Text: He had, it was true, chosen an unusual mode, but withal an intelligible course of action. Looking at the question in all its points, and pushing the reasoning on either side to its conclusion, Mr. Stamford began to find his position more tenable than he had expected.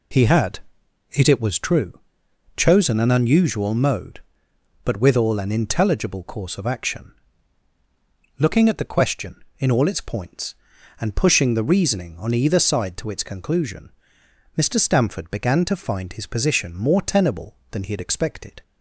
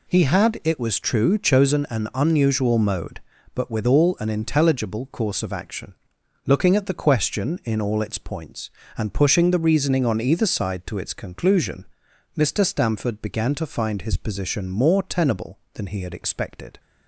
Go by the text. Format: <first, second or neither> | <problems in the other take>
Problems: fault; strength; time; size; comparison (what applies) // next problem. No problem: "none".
second | says "it" twice; at 1.2 s